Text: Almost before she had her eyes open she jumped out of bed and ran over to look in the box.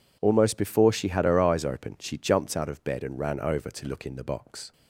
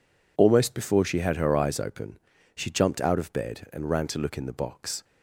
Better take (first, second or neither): first